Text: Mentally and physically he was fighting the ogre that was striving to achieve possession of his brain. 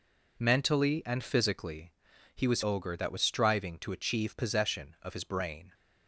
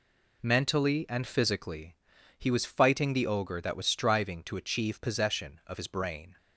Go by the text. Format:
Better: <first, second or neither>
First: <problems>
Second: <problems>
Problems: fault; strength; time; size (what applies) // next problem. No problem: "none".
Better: second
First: pauses between "physically" and "he"; at 1.9 s; 0.42 s long // skips "fighting the"; at 2.6 s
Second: pauses between "physically" and "he"; at 1.9 s; 0.42 s long